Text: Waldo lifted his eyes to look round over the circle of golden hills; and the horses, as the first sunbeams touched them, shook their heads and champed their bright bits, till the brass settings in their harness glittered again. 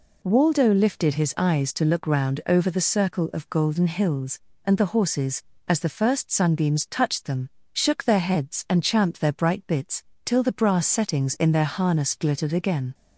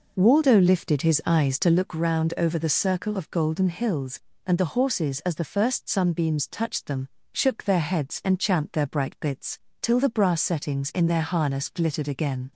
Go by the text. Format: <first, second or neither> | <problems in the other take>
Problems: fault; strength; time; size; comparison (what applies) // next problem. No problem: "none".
first | starts louder than the rest; noticeable; until 1.9 s; 5 dB